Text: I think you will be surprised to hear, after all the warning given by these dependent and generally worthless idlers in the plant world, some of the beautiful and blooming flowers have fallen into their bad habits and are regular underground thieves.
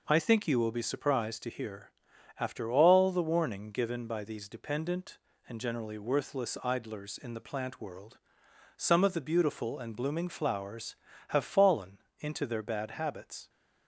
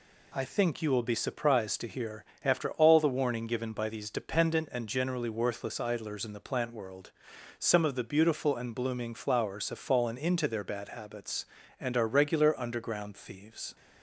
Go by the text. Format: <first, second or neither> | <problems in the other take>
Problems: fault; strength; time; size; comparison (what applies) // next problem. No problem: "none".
second | pauses between "fallen" and "into"; slight; at 11.9 s; 0.22 s long // stops before "and are regular underground thieves"; at 13.4 s